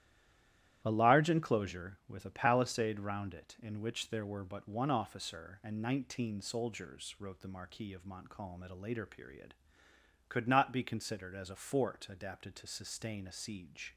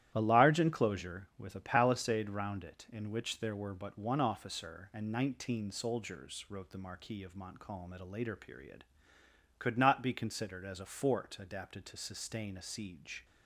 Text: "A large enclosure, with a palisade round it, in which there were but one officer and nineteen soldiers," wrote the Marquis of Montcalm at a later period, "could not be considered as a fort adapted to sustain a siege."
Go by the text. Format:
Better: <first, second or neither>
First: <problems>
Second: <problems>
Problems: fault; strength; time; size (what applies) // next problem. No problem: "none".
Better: second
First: stays silent before the first word; slight; until 0.8 s; 0.8 s long // starts louder than the rest; strong; until 1.8 s; 12.5 dB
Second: starts louder than the rest; strong; until 1.1 s; 12.5 dB